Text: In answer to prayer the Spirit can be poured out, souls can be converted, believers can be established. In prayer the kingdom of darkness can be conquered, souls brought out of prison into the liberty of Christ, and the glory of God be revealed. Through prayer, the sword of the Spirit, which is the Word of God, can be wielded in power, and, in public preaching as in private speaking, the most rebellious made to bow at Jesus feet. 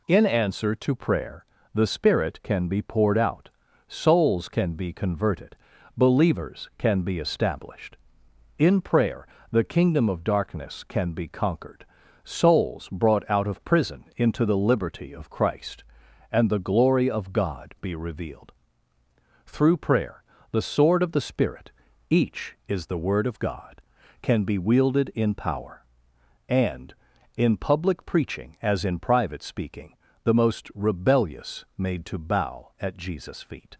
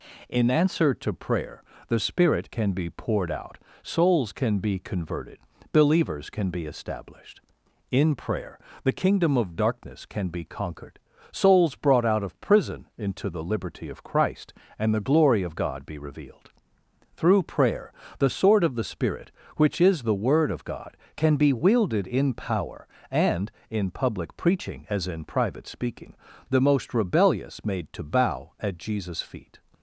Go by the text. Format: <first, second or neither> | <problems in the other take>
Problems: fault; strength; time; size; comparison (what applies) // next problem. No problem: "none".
second | pauses between "prayer" and "the"; slight; at 1.4 s; 0.28 s long; slight in the second // pauses between "prayer" and "the"; slight; at 9.2 s; 0.24 s long; slight in the second // says "each" for "which"; at 22.0 s